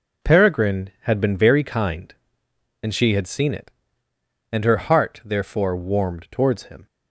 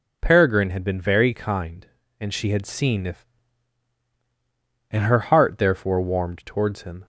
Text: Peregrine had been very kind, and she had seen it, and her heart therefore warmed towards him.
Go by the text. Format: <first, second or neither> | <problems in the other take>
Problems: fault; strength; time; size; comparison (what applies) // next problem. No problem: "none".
first | says "if" for "it"; at 3.0 s